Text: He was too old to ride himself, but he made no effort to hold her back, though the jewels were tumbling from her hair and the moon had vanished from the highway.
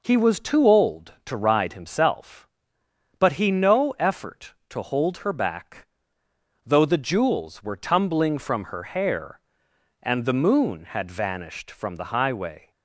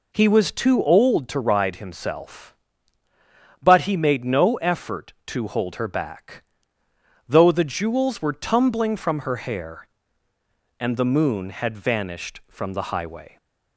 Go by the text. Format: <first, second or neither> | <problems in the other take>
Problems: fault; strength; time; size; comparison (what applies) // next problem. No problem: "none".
second | skips "made"; at 3.5 s